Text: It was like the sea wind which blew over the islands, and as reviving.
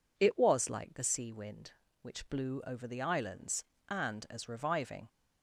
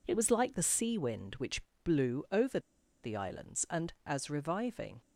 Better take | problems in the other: first | pauses between "which" and "blew"; slight; at 1.6 s; 0.22 s long // pauses between "over" and "the"; at 2.5 s; 0.43 s long

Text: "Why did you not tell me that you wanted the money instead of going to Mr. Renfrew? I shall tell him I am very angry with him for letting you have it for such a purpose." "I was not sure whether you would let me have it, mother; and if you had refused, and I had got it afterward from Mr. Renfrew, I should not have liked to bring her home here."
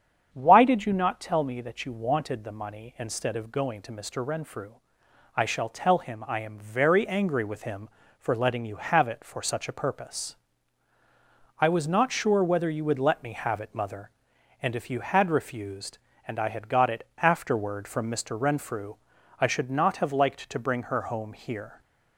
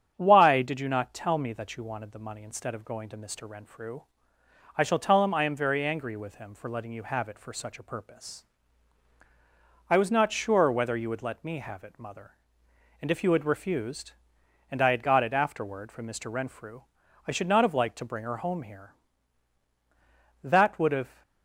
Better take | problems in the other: first | starts louder than the rest; strong; until 1.1 s; 8.5 dB; strong in the first // goes on to say "That would have"; noticeable; from 20.4 s on; 0.78 s long

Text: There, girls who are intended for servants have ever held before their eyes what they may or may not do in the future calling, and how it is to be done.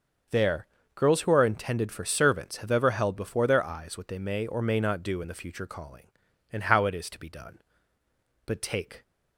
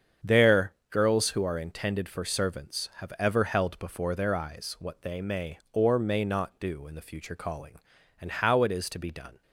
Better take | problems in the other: second | starts louder than the rest; until 1.6 s; 6.5 dB; strong in the second // goes on to say "But take"; from 8.4 s on; 0.58 s long

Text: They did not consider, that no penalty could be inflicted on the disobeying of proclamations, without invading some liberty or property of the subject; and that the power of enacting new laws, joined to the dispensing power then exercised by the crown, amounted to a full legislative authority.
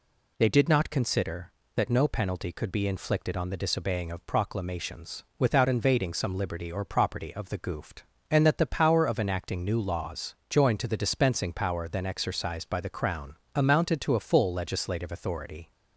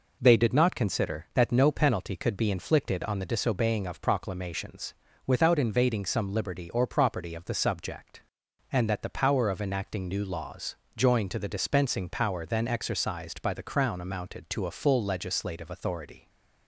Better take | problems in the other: second | says "goofed" for "subject"; at 7.5 s

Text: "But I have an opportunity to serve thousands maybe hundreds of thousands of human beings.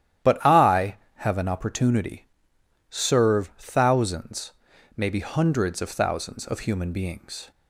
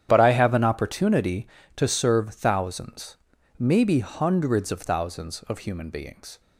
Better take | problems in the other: second | starts louder than the rest; strong; until 1.4 s; 11.5 dB; strong in the second // skips "to"; at 2.5 s // pauses between "thousands" and "maybe"; noticeable; at 4.5 s; 0.46 s long; also in the second

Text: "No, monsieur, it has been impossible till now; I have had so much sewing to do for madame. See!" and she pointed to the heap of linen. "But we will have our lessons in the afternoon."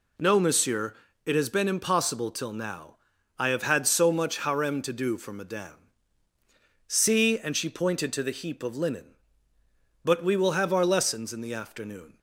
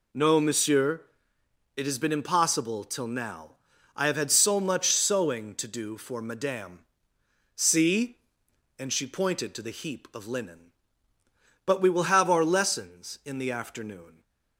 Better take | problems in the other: second | says "harem" for "sewing"; at 4.3 s

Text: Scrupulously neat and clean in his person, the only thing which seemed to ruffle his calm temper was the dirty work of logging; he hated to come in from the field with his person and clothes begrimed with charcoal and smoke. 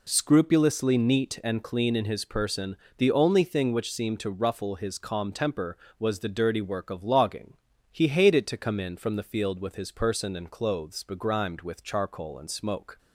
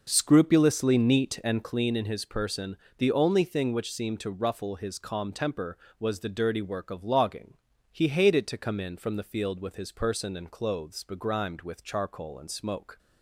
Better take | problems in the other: first | starts louder than the rest; noticeable; until 1.9 s; 5.5 dB

